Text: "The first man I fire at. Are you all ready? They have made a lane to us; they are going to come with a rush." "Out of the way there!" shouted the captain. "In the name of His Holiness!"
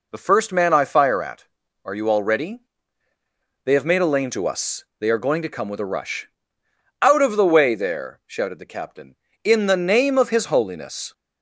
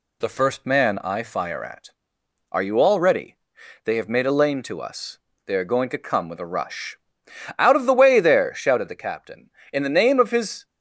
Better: first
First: none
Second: stops before "Holiness"; at 10.6 s

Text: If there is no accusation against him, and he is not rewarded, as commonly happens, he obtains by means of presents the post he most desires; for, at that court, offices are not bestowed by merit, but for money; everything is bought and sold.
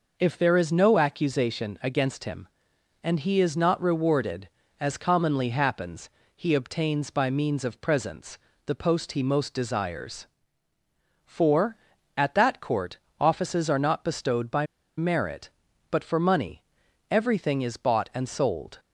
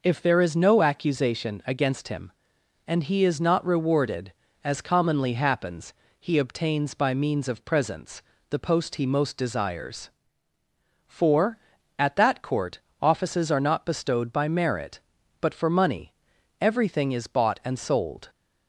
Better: second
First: pauses between "presents" and "the"; slight; at 8.3 s; 0.26 s long // pauses between "by" and "merit"; slight; at 14.6 s; 0.32 s long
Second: pauses between "presents" and "the"; slight; at 8.2 s; 0.26 s long

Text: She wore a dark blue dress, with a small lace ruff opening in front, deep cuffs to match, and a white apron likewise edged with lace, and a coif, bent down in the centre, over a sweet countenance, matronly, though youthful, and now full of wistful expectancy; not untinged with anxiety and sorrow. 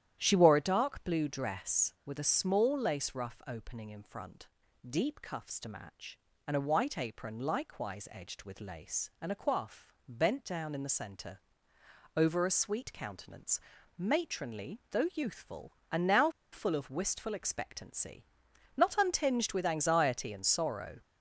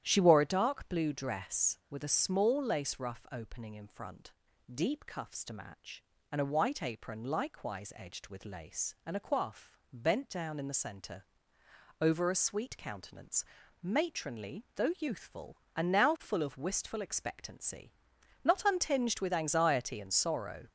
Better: second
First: starts louder than the rest; strong; until 1.2 s; 11 dB // pauses between "now" and "full"; slight; at 16.3 s; 0.22 s long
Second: starts louder than the rest; strong; until 1.0 s; 11 dB

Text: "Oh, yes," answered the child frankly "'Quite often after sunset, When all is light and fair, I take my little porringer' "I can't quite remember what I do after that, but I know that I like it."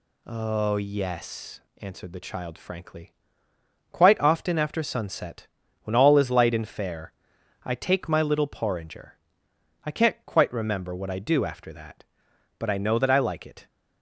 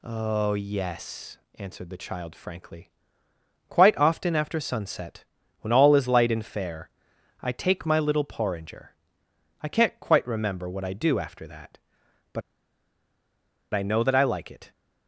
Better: first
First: pauses between "frankly" and "Quite"; noticeable; at 3.1 s; 0.78 s long // pauses between "porringer" and "I"; noticeable; at 9.1 s; 0.68 s long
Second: pauses between "frankly" and "Quite"; noticeable; at 2.9 s; 0.78 s long // pauses between "porringer" and "I"; noticeable; at 8.9 s; 0.68 s long // pauses between "but" and "I"; strong; at 12.4 s; 1.3 s long

